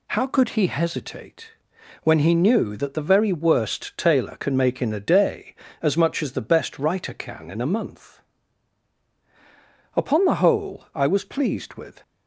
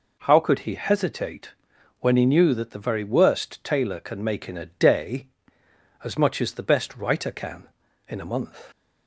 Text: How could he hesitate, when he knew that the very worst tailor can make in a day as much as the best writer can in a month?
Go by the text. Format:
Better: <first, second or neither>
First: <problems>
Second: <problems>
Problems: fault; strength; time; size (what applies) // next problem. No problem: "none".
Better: second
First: goes on to say "Upon the whole I was pleased with"; strong; from 9.9 s on; 2.0 s long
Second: none